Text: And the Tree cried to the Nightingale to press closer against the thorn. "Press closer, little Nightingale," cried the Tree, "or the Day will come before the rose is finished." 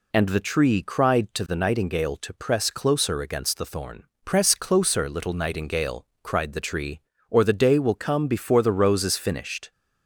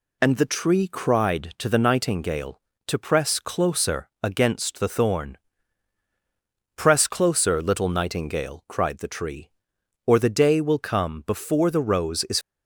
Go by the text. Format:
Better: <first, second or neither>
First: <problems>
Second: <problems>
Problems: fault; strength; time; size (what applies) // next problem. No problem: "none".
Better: first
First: none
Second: stops before "finished"; at 12.4 s